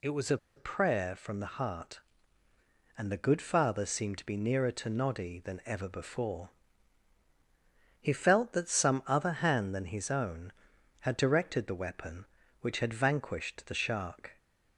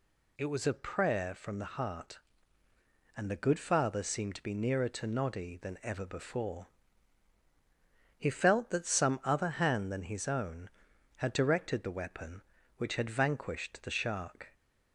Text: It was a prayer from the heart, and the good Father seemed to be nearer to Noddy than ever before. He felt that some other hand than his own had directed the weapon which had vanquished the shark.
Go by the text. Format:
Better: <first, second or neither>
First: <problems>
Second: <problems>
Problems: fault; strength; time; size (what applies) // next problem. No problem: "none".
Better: second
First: pauses between "a" and "prayer"; slight; at 0.3 s; 0.19 s long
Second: none